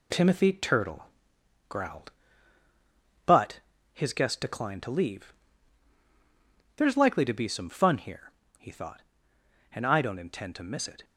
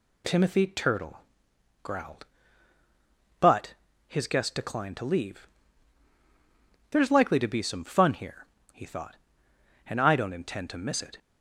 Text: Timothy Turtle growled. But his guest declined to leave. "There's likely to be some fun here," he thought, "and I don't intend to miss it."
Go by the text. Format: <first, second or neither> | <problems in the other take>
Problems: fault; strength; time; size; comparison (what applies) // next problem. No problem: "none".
second | gets quieter; noticeable; throughout; 5 dB // pauses between "Turtle" and "growled"; noticeable; at 1.0 s; 0.64 s long; noticeable in the second // pauses between "But" and "his"; slight; at 3.6 s; 0.32 s long; slight in the second